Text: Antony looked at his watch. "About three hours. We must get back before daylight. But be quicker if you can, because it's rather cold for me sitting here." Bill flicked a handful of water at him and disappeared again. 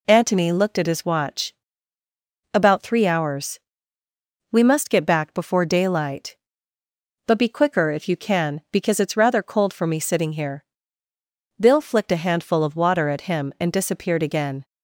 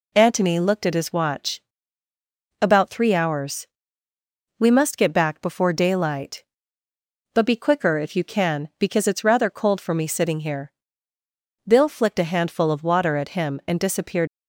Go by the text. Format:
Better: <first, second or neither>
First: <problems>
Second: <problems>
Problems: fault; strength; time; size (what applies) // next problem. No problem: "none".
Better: first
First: none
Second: stops before "again"; at 14.2 s